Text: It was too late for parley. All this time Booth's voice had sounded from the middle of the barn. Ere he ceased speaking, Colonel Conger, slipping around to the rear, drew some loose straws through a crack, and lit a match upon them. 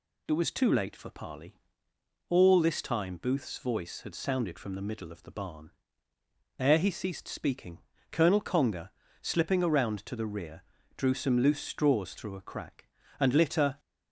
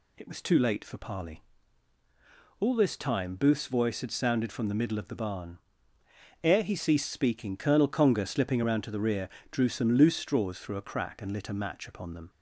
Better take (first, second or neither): second